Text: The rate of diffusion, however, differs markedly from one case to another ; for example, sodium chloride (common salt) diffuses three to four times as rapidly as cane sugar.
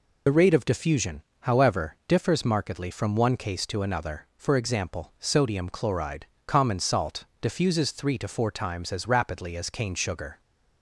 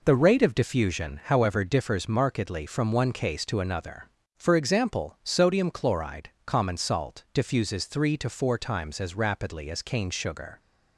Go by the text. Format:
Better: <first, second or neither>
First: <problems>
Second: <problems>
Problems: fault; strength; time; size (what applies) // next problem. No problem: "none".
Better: second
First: loses the start of "The"; at 0.2 s; 50 ms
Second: none